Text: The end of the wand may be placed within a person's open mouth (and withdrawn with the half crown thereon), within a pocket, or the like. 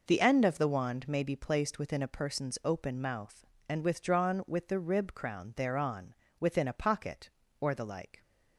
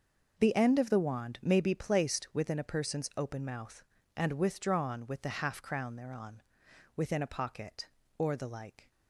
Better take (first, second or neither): second